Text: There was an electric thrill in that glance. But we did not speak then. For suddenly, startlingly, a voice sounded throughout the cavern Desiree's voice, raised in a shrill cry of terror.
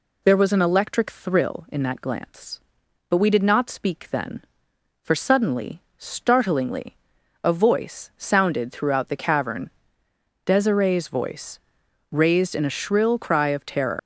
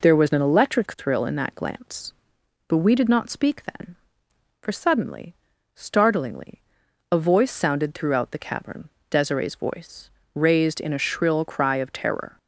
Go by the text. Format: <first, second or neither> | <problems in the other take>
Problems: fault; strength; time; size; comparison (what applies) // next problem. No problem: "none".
second | pauses between "cavern" and "Desiree's"; noticeable; at 9.6 s; 0.76 s long; slight in the second // leaves "terror" unfinished; at 13.9 s; 130 ms